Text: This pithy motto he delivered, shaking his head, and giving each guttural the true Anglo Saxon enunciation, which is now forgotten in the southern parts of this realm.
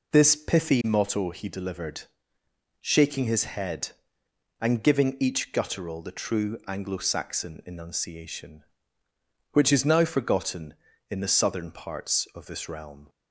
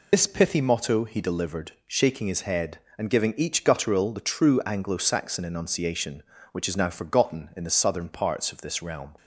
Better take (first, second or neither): first